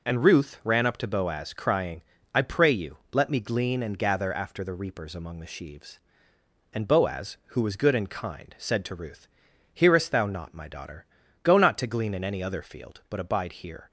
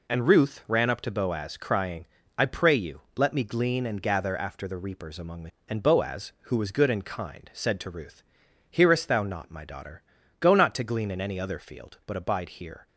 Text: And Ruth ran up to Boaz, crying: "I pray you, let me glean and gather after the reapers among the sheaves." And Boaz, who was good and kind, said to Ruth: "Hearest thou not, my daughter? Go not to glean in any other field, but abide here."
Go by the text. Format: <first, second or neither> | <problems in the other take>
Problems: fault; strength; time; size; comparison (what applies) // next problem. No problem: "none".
first | skips "sheaves"; at 5.5 s